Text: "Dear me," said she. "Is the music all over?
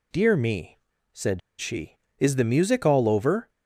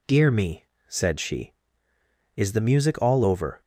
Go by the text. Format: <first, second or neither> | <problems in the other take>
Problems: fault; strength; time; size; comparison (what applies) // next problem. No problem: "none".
second | pauses between "said" and "she"; slight; at 1.4 s; 0.18 s long